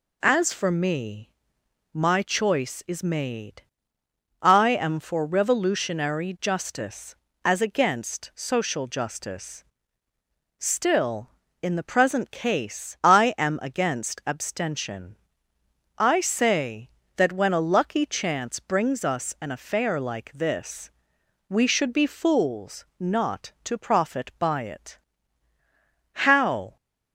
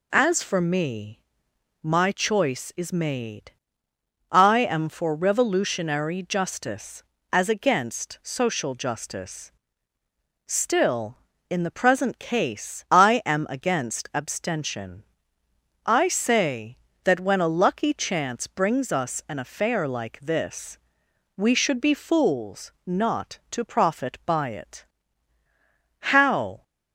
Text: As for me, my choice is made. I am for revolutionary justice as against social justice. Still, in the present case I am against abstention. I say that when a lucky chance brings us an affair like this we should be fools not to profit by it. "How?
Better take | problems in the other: neither | pauses between "this" and "we"; noticeable; the same in both

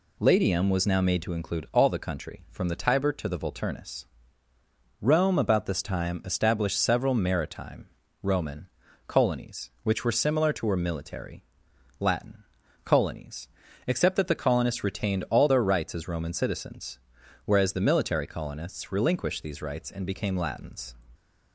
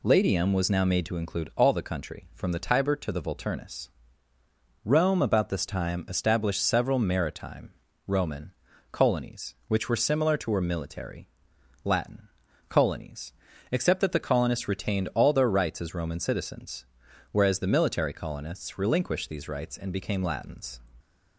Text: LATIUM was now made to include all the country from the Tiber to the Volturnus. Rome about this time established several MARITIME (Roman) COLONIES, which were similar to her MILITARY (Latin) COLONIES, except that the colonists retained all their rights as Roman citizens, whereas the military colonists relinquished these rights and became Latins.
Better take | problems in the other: neither | none

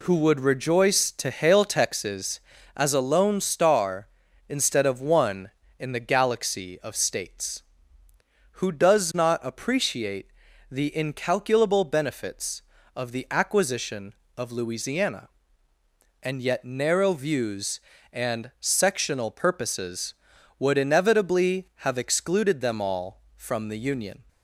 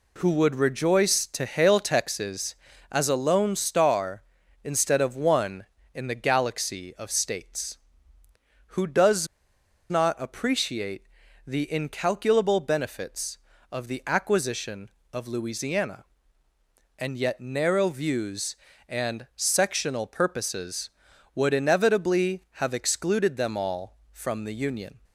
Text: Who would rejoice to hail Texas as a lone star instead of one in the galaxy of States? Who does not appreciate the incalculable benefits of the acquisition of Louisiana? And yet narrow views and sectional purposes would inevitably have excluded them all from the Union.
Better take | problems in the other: first | pauses between "does" and "not"; noticeable; at 9.2 s; 0.63 s long // pauses between "appreciate" and "the"; at 11.0 s; 0.44 s long; also in the first

